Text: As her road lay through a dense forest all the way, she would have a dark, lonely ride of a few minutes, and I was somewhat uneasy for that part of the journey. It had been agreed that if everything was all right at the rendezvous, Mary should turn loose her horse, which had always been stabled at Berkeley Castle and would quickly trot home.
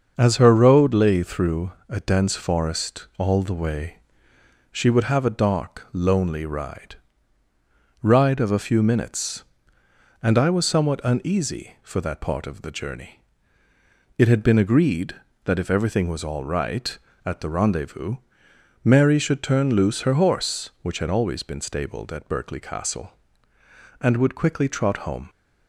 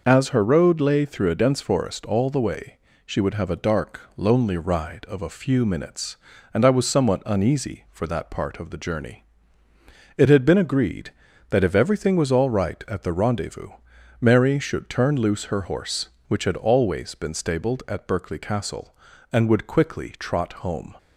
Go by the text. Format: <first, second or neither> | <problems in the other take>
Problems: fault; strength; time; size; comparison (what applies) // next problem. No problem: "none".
second | starts louder than the rest; until 1.1 s; 6.5 dB // pauses between "through" and "a"; slight; at 1.7 s; 0.18 s long // says "ride" twice; at 8.0 s